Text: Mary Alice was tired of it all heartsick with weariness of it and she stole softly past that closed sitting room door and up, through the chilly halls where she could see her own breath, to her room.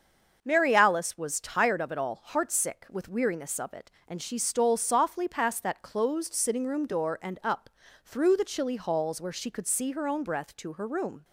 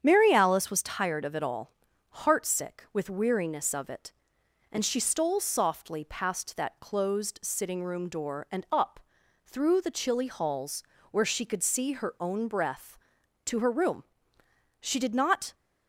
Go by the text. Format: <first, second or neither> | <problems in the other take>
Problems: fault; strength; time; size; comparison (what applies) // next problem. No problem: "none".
first | starts louder than the rest; strong; until 1.0 s; 8 dB; also in the first // pauses between "all" and "heartsick"; noticeable; at 1.7 s; 0.54 s long // pauses between "halls" and "where"; slight; at 10.8 s; 0.30 s long // goes on to say "She did not"; noticeable; from 14.7 s on; 0.74 s long